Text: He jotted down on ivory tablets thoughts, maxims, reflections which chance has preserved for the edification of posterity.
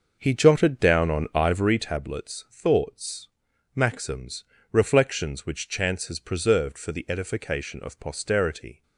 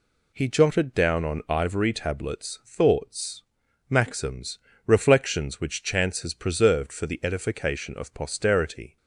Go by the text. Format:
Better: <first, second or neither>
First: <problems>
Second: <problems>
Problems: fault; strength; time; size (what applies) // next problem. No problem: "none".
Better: second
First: starts louder than the rest; noticeable; until 2.0 s; 6 dB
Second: none